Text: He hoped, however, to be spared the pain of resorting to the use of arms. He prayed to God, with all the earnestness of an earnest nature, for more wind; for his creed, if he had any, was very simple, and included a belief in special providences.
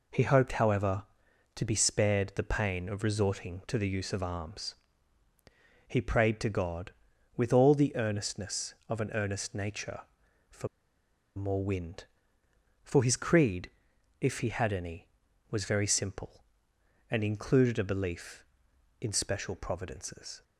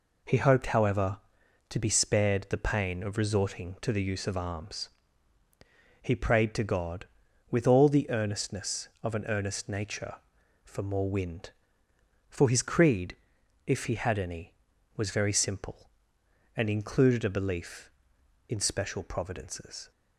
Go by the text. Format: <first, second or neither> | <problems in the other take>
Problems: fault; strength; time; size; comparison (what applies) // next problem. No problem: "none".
second | pauses between "for" and "more"; noticeable; at 10.6 s; 0.69 s long